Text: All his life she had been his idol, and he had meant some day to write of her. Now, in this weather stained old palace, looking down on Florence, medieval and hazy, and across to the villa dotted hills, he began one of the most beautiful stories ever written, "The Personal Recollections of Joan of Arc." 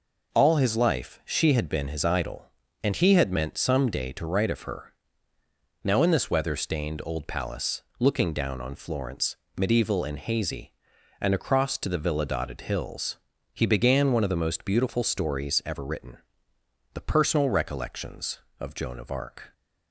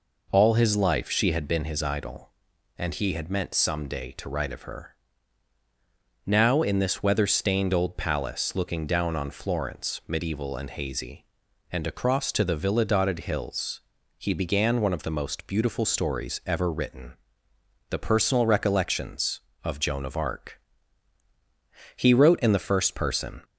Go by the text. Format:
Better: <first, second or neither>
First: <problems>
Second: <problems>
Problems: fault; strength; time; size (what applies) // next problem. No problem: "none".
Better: first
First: none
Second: goes on to say "He wrote in the first person"; from 21.9 s on; 1.4 s long